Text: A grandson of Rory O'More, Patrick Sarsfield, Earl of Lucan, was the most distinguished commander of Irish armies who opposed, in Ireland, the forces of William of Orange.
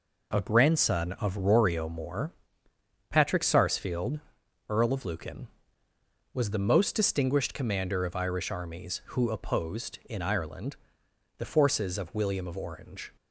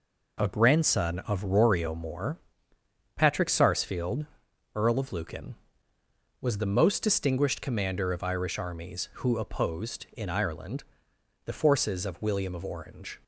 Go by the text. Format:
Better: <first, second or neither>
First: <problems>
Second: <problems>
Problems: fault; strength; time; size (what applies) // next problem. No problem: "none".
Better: neither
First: none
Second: none